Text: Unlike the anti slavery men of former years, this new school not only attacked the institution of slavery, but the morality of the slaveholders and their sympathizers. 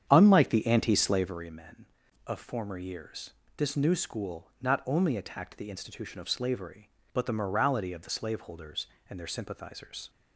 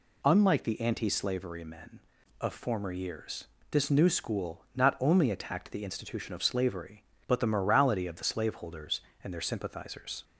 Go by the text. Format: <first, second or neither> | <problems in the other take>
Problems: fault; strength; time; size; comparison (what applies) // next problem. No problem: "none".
second | starts louder than the rest; strong; until 1.5 s; 8.5 dB